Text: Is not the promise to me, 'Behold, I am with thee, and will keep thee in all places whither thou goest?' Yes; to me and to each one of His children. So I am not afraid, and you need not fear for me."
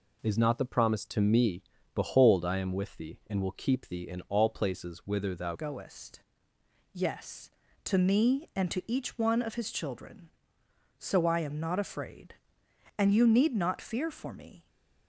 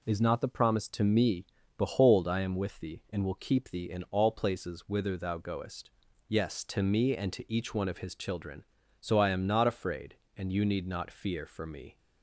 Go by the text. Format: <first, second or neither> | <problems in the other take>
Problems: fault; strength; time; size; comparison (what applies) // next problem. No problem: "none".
second | changes voice at "goest"; from 5.5 s on; 9.1 s long